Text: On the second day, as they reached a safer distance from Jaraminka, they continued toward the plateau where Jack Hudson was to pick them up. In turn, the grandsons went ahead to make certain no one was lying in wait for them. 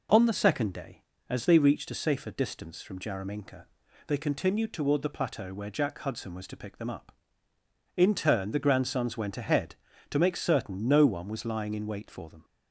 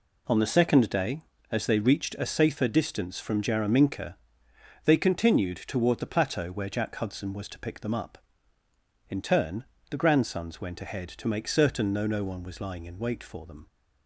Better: first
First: none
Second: says "no" twice; at 12.0 s

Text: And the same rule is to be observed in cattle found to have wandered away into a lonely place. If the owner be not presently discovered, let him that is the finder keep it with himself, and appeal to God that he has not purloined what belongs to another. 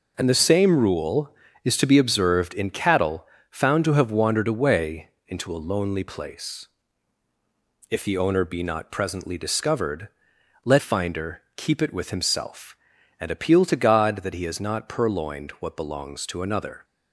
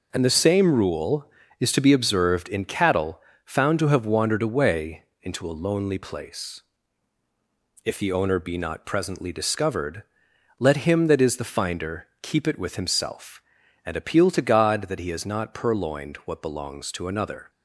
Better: second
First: pauses between "cattle" and "found"; slight; at 3.2 s; 0.26 s long // pauses between "away" and "into"; slight; at 5.0 s; 0.18 s long // skips "him that is the"; at 10.7 s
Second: pauses between "cattle" and "found"; slight; at 3.1 s; 0.26 s long // pauses between "away" and "into"; slight; at 5.0 s; 0.18 s long

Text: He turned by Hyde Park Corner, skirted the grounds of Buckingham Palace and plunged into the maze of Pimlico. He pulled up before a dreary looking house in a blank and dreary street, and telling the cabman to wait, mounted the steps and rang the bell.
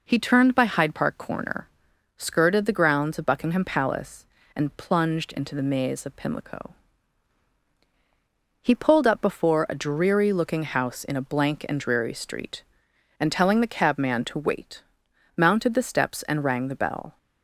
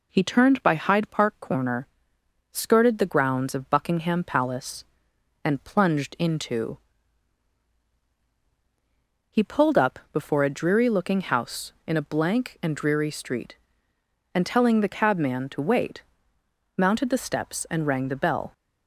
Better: first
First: none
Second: skips "the maze of Pimlico"; at 8.0 s

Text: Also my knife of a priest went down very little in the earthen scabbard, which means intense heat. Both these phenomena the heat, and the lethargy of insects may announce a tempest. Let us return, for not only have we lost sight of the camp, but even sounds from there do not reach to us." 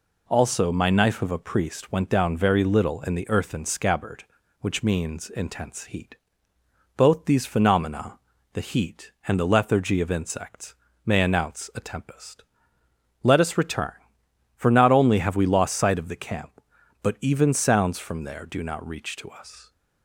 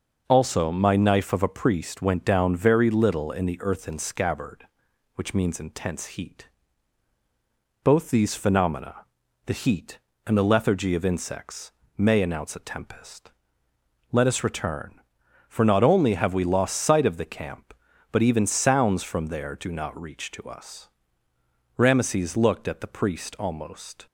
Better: first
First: pauses between "phenomena" and "the"; slight; at 8.1 s; 0.36 s long // pauses between "insects" and "may"; slight; at 10.7 s; 0.30 s long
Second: pauses between "phenomena" and "the"; noticeable; at 8.9 s; 0.46 s long // pauses between "insects" and "may"; slight; at 11.6 s; 0.28 s long // goes on to say "Rameses looked at the priest almost"; strong; from 21.7 s on; 2.3 s long

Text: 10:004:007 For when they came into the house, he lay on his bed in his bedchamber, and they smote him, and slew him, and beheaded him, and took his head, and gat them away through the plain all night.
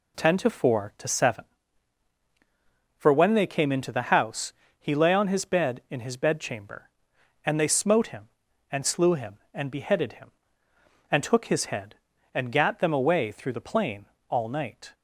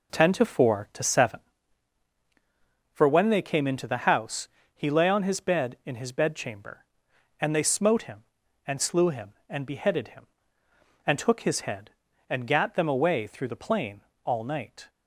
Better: first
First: pauses between "plain" and "all"; slight; at 14.0 s; 0.24 s long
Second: starts louder than the rest; until 1.9 s; 4 dB // pauses between "plain" and "all"; slight; at 14.0 s; 0.24 s long

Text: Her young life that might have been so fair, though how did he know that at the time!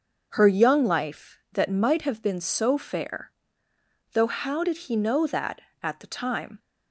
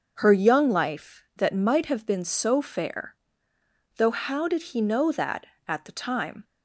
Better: neither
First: starts louder than the rest; until 1.3 s; 6.5 dB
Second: starts louder than the rest; until 1.1 s; 6.5 dB

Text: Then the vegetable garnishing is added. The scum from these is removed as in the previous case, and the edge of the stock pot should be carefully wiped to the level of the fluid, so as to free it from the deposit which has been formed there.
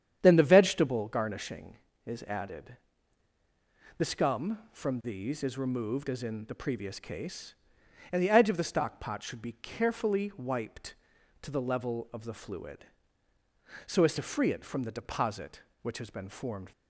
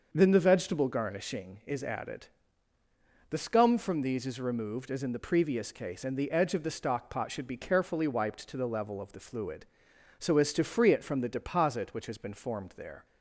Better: second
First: starts louder than the rest; strong; until 1.2 s; 9 dB // stops before "there"; at 16.7 s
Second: starts louder than the rest; until 1.1 s; 6 dB

